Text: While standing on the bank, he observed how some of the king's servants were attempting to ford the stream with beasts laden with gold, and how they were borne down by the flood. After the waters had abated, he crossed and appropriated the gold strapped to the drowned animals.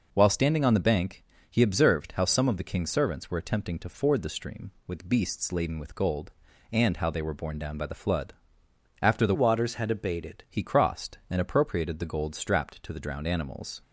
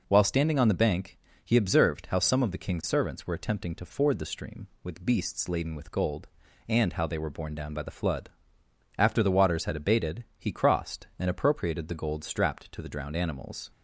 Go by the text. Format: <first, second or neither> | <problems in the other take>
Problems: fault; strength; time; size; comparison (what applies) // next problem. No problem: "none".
second | changes voice from "waters" to "abated"; from 9.3 to 10.4 s; 1.1 s long